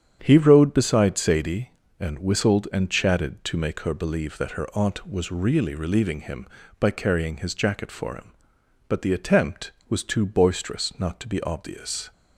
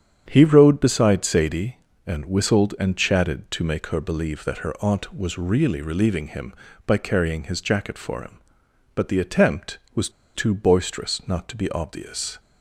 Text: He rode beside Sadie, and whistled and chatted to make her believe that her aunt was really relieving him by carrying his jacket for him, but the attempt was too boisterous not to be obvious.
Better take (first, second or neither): first